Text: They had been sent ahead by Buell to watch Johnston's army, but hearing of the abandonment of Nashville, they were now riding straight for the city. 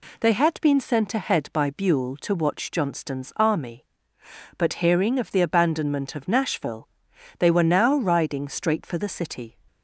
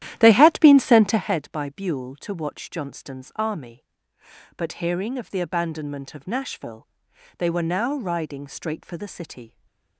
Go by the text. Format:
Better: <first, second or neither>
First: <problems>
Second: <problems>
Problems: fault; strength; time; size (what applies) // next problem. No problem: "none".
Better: first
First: none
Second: starts louder than the rest; strong; until 1.4 s; 12.5 dB // stays silent after the last word; slight; from 9.4 s on; 0.5 s long